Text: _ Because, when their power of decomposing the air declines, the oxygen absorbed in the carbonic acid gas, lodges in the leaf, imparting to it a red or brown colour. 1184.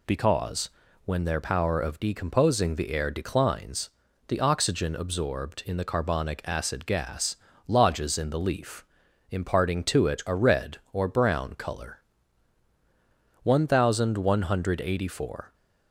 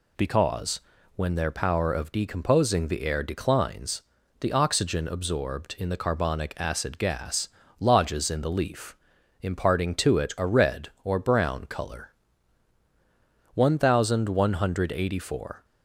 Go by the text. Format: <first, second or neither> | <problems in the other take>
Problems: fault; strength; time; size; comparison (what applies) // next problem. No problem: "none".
neither | none